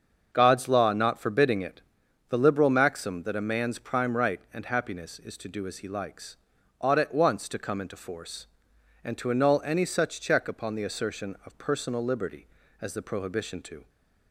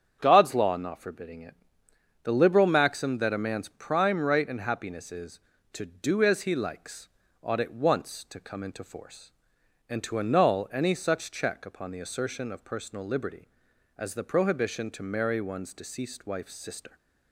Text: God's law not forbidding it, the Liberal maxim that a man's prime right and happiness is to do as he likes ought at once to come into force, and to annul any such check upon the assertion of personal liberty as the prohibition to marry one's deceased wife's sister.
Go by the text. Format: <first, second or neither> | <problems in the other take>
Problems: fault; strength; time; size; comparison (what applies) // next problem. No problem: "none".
second | starts louder than the rest; until 1.3 s; 6.5 dB; strong in the second // pauses between "likes" and "ought"; at 6.3 s; 0.42 s long; slight in the second // stops before "marry one's deceased wife's sister"; at 13.8 s